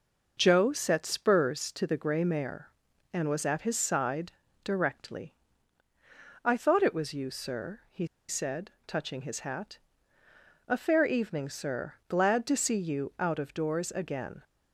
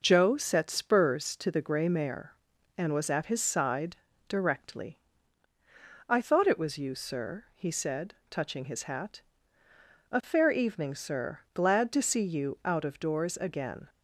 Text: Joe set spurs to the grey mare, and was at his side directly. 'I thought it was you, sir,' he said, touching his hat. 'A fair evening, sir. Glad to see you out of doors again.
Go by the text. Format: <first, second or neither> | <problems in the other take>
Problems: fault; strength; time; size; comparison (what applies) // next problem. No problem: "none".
second | pauses between "side" and "directly"; slight; at 4.3 s; 0.32 s long; slight in the second // pauses between "he" and "said"; slight; at 8.0 s; 0.22 s long